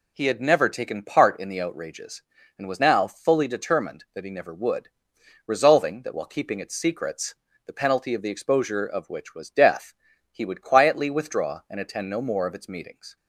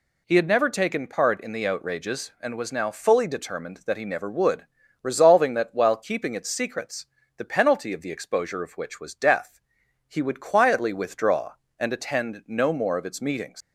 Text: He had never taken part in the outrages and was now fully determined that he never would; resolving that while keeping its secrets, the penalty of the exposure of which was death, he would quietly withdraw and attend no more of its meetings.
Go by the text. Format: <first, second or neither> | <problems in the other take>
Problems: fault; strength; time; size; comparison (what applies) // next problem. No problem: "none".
first | leaves "meetings" unfinished; at 13.6 s; 85 ms